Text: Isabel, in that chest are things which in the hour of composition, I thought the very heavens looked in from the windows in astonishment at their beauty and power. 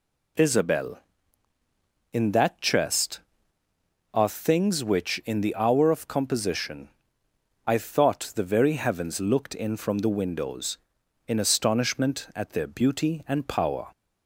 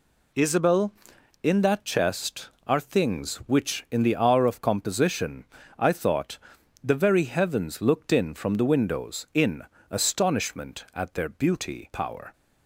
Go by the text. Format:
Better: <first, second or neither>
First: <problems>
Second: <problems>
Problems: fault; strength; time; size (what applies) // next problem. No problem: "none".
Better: first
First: none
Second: pauses between "thought" and "the"; noticeable; at 6.3 s; 0.46 s long // pauses between "in" and "astonishment"; slight; at 9.6 s; 0.28 s long // skips "and"; at 11.9 s